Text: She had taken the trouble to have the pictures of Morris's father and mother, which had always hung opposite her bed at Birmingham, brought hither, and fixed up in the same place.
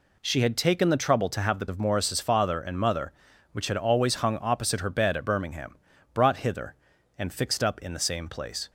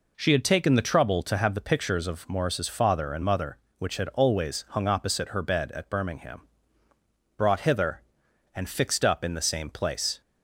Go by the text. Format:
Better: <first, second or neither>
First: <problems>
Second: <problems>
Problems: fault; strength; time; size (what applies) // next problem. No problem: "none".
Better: second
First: skips "pictures"; at 1.6 s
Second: none